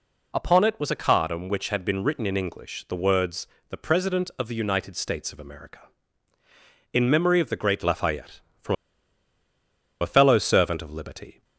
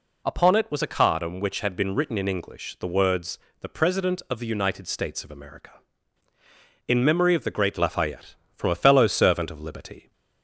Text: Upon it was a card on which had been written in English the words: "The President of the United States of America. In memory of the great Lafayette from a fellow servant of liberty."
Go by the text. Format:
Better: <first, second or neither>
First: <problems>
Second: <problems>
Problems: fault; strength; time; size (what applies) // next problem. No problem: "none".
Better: second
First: pauses between "from" and "a"; strong; at 8.7 s; 1.2 s long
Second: none